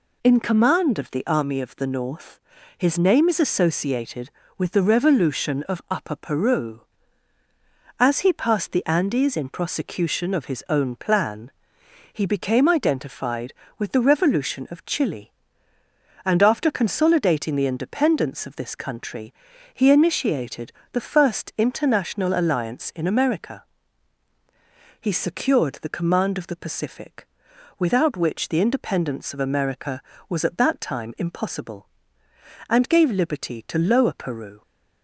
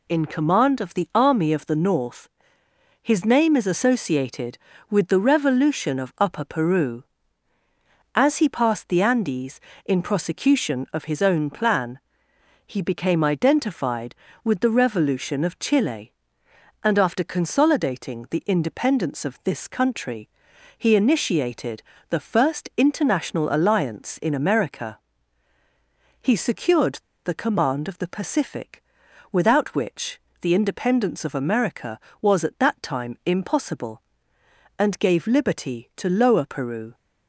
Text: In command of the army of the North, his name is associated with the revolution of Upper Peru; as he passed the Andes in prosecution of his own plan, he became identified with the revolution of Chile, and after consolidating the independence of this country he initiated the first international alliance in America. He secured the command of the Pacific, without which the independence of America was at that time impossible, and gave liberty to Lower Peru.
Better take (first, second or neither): first